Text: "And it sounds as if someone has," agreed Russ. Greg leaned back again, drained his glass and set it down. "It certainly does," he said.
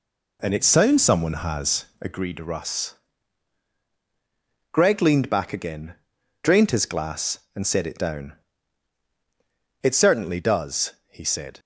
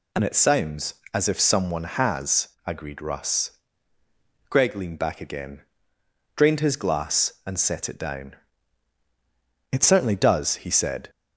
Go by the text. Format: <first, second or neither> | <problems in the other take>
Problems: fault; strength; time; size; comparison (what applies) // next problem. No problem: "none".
second | skips "as if"; at 1.0 s